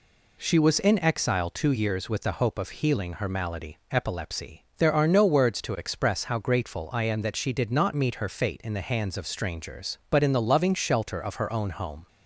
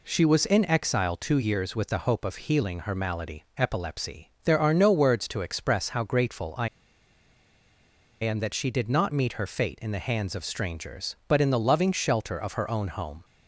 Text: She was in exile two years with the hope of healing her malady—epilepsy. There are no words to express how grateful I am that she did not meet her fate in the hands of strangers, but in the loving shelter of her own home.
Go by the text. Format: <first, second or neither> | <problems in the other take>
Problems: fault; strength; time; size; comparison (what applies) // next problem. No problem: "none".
first | pauses between "I" and "am"; strong; at 6.6 s; 1.5 s long